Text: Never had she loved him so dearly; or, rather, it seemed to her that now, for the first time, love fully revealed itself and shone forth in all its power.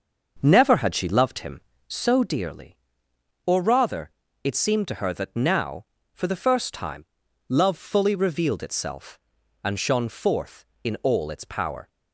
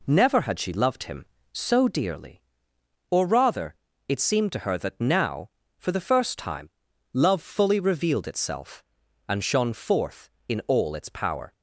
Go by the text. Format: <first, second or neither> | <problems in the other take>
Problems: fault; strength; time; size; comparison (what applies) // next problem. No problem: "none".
second | starts louder than the rest; noticeable; until 1.5 s; 6 dB